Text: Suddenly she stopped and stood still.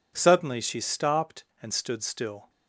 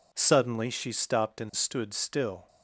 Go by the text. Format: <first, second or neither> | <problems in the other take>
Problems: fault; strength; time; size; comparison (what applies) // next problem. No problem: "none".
neither | none